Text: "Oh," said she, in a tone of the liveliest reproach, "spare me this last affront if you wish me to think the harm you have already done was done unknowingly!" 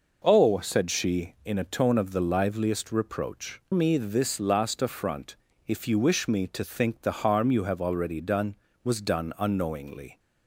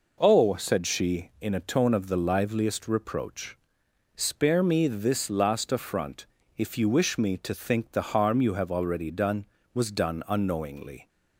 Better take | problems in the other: second | skips "spare"; at 3.6 s // pauses between "affront" and "if"; slight; at 5.3 s; 0.32 s long; slight in the second

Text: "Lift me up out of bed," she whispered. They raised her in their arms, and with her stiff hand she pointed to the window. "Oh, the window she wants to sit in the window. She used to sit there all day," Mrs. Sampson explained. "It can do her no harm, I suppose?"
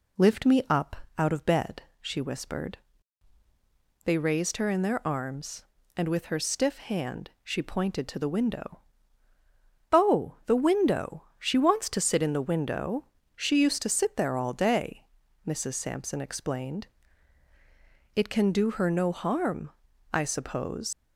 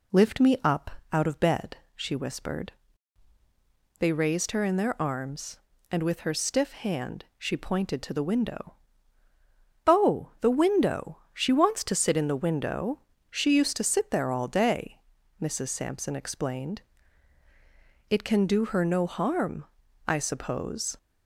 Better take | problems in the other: second | pauses between "up" and "out"; slight; at 0.9 s; 0.22 s long; slight in the second // leaves "suppose" unfinished; at 20.9 s; 95 ms

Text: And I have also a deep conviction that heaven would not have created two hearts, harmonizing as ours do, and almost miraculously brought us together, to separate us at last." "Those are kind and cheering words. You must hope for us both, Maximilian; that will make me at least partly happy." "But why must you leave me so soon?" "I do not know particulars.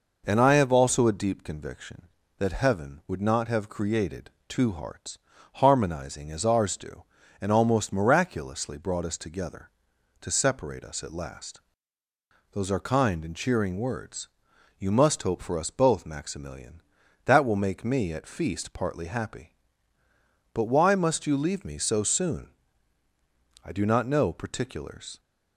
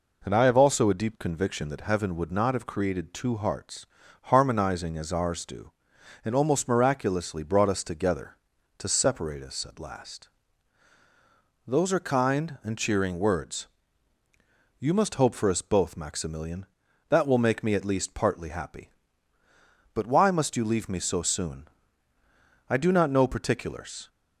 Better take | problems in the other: second | pauses between "created" and "two"; slight; at 4.2 s; 0.18 s long // says "feast" for "least"; at 18.2 s

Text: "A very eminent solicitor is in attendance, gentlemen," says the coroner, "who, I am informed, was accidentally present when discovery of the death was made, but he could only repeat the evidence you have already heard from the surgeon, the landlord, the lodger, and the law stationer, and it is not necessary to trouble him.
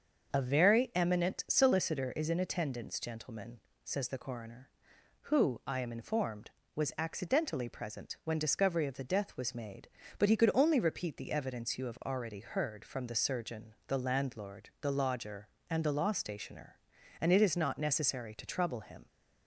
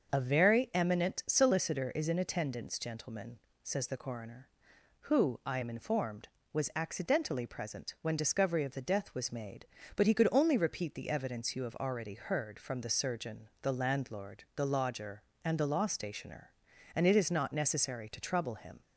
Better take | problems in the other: neither | starts louder than the rest; the same in both

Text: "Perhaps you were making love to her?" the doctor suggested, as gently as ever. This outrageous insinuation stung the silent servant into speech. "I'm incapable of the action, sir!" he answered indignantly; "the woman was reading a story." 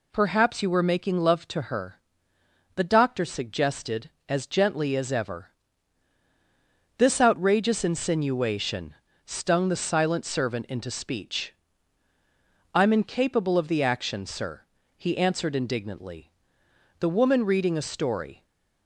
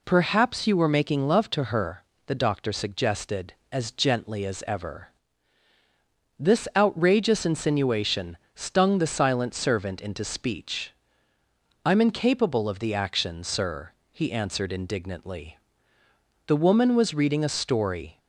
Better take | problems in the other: second | pauses between "insinuation" and "stung"; slight; at 8.9 s; 0.32 s long; slight in the second // skips "was"; at 17.4 s

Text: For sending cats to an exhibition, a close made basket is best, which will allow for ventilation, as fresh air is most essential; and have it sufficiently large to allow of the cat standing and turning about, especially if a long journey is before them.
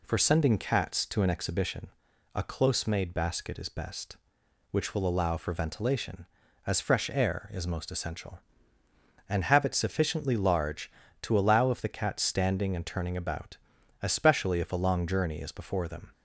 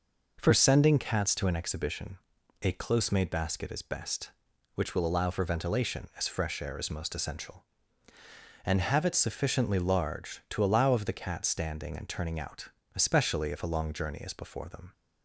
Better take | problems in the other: first | says "out" for "about"; at 12.3 s

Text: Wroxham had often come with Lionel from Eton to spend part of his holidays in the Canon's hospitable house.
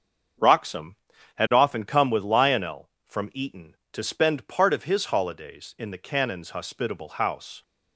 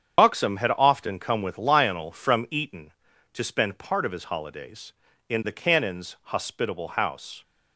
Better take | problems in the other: first | loses the start of "Wroxham"; at 0.1 s; 115 ms // starts louder than the rest; strong; until 1.2 s; 8 dB; also in the first

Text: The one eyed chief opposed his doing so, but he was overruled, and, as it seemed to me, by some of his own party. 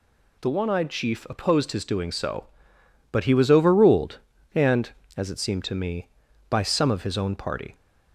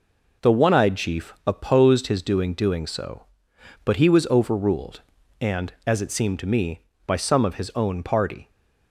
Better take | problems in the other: first | says "doing" twice; at 2.5 s

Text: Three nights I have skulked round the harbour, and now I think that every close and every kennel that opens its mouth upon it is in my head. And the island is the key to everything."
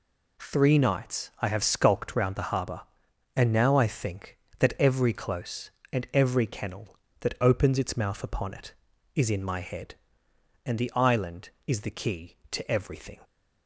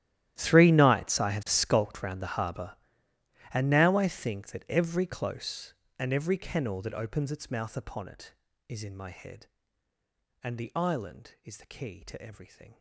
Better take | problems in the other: first | gets quieter; strong; throughout; 21 dB

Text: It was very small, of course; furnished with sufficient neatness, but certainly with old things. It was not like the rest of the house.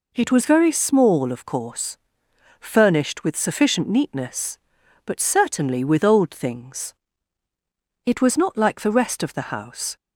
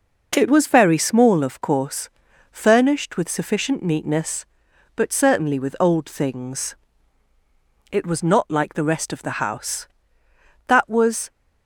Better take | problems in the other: first | goes on to say "That was"; noticeable; from 10.6 s on; 0.64 s long

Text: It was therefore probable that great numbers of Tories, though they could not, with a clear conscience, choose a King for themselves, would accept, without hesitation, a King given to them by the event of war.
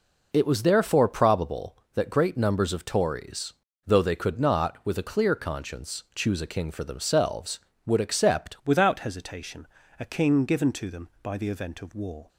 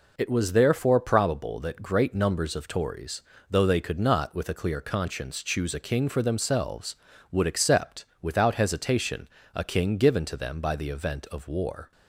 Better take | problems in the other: second | changes voice at "without"; from 8.6 s on; 3.6 s long

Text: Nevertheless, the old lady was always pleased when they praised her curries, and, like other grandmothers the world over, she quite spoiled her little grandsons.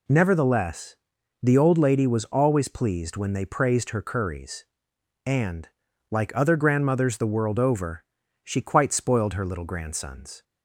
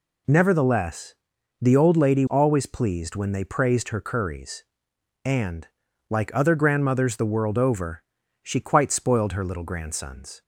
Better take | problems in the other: first | skips "was"; at 2.2 s

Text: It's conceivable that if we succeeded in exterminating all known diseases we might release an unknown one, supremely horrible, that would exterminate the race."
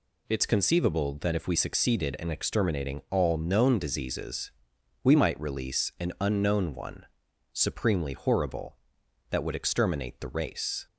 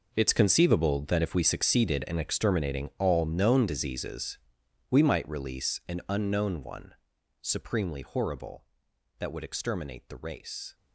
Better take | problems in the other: first | gets quieter; strong; throughout; 15.5 dB // pauses between "diseases" and "we"; noticeable; at 4.3 s; 0.50 s long; noticeable in the first

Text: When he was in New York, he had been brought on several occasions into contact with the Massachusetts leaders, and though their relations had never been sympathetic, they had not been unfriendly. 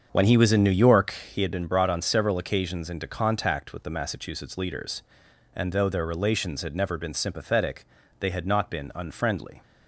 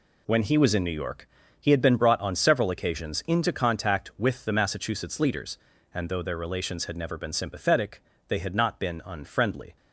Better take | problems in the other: second | starts louder than the rest; strong; until 1.5 s; 7.5 dB

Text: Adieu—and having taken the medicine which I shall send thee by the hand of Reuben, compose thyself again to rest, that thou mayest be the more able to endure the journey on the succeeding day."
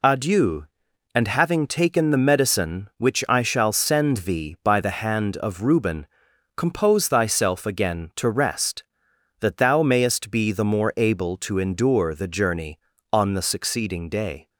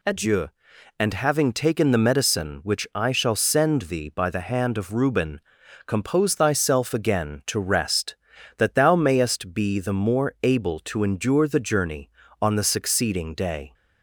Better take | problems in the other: neither | none

